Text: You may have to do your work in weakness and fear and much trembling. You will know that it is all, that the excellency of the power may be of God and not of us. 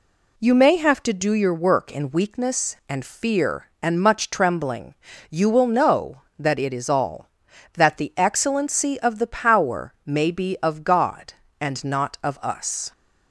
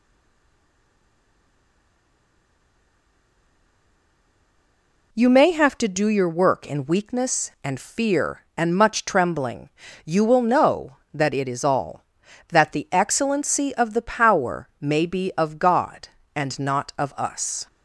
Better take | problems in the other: first | stays silent before the first word; strong; until 5.1 s; 5.1 s long

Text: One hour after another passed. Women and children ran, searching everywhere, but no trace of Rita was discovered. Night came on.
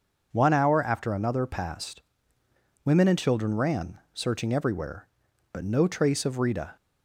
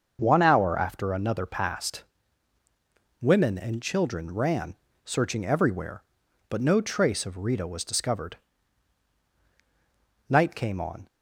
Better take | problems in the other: second | starts louder than the rest; until 1.3 s; 6.5 dB; also in the second // stops before "was discovered Night came on"; at 6.7 s

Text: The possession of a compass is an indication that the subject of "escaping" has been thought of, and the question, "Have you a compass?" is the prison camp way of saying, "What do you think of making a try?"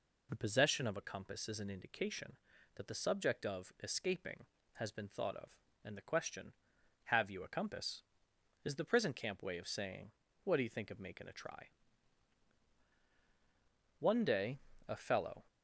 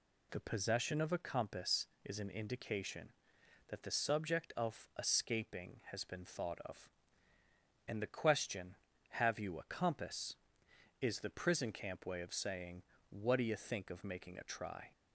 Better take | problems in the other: second | goes on to say "One day a fellow"; from 13.9 s on; 1.4 s long

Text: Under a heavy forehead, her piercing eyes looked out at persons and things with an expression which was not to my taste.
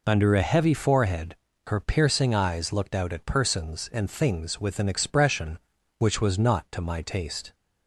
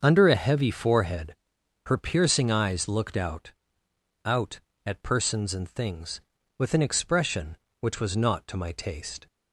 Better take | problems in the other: first | starts louder than the rest; until 1.0 s; 6.5 dB // says "out" twice; at 4.2 s

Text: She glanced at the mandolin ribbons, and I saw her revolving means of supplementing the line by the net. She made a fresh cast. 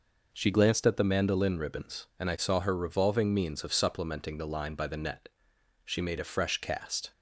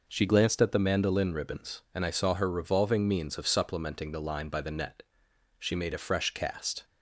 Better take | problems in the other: neither | none

